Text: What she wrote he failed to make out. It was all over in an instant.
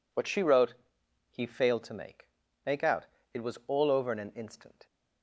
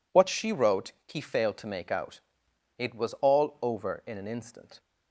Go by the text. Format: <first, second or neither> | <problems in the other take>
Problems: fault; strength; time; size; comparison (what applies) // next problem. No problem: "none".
second | pauses between "wrote" and "he"; noticeable; at 0.7 s; 0.56 s long; slight in the second // says "make" twice; at 2.6 s